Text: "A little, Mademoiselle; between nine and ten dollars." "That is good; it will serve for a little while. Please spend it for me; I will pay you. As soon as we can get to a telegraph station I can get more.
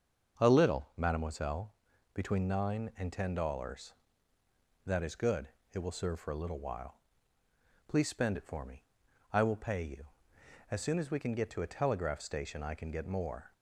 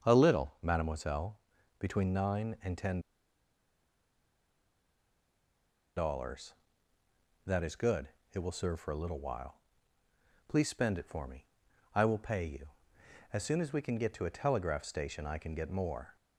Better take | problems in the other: first | starts louder than the rest; until 1.0 s; 6.5 dB; also in the first // pauses between "ten" and "dollars"; strong; at 2.9 s; 2.9 s long

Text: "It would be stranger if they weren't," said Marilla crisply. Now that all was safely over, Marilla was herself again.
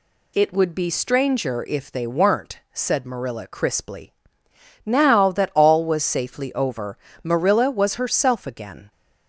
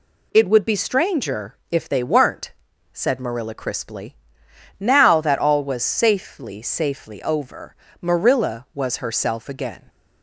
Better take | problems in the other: first | pauses between "stranger" and "if"; slight; at 1.5 s; 0.16 s long // says "safely" twice; at 6.6 s

